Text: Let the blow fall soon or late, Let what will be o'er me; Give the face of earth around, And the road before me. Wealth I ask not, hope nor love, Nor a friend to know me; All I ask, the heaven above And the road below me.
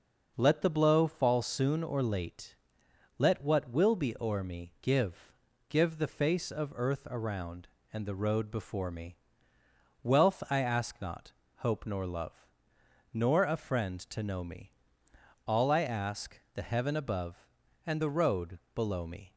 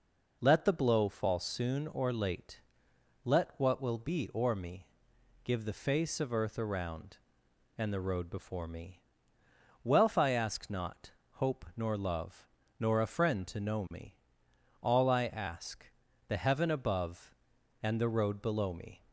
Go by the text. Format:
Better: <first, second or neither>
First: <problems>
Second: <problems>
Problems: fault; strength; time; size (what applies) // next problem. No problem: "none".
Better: second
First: says "Give" twice; at 5.6 s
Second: none